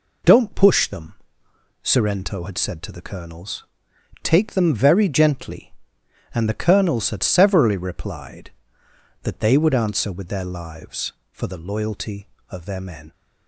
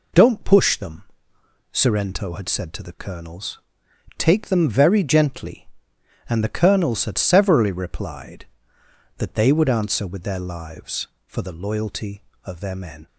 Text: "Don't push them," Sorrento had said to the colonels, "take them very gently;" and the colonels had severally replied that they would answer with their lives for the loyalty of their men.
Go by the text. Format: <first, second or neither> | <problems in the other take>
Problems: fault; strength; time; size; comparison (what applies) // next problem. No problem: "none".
neither | none